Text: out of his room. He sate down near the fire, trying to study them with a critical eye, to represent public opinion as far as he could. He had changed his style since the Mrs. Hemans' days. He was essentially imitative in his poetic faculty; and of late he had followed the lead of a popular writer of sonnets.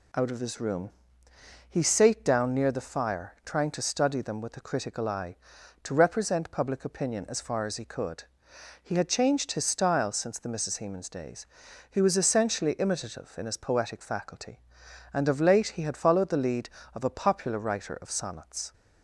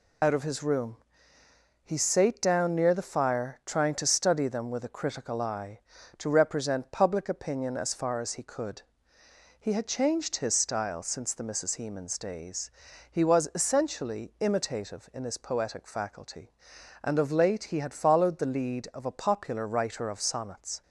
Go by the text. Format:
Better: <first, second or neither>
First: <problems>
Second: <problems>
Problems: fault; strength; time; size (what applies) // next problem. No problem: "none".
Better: first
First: none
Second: loses the start of "out"; at 0.2 s; 40 ms